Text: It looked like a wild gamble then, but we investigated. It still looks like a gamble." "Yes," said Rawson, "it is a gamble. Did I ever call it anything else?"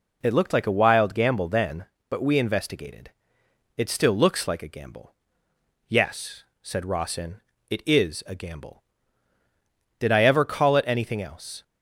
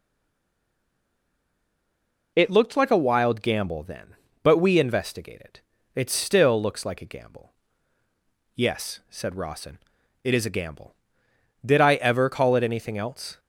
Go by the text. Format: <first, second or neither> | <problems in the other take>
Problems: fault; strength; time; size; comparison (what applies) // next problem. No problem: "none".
first | stays silent before the first word; until 2.3 s; 2.3 s long